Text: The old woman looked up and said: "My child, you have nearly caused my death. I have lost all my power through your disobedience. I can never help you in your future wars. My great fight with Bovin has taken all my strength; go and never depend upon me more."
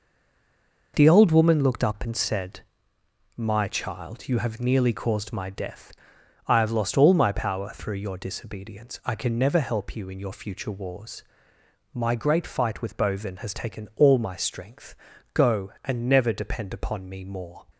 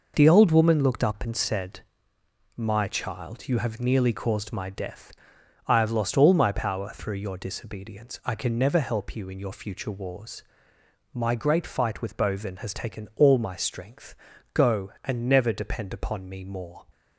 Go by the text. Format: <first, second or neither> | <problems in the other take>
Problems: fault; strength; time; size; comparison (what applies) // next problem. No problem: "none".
second | stays silent before the first word; slight; until 0.9 s; 0.9 s long